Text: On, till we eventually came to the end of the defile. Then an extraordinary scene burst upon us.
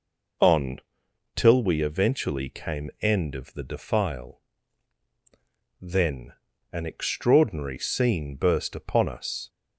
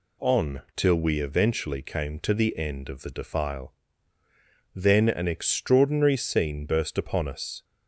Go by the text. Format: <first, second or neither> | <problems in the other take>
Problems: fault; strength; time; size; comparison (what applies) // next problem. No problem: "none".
second | skips "to the"; at 2.9 s // pauses between "Then" and "an"; at 6.3 s; 0.38 s long